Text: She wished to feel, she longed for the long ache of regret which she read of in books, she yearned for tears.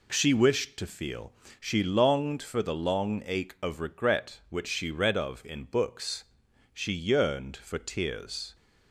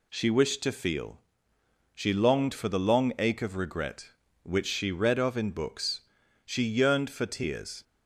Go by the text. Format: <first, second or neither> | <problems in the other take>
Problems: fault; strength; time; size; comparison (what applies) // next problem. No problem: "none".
neither | none